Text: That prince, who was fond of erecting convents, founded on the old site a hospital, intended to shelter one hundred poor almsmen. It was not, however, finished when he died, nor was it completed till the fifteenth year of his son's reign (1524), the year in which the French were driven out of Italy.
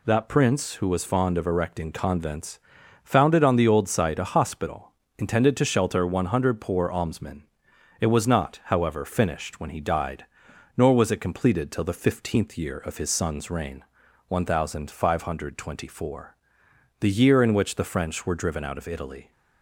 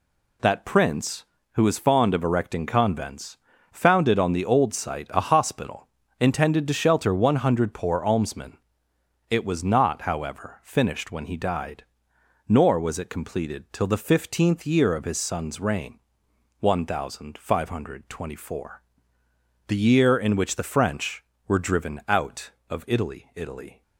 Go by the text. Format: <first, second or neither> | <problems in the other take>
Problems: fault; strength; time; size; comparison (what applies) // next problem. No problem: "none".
first | says "Italy" twice; at 23.3 s